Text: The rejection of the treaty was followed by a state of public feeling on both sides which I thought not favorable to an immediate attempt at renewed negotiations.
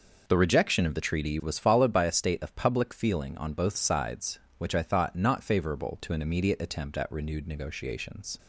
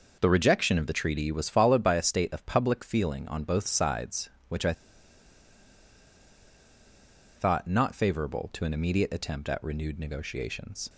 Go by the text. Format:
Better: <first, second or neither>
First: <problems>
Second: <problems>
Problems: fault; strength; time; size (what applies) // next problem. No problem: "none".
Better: first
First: none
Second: pauses between "I" and "thought"; strong; at 4.7 s; 2.6 s long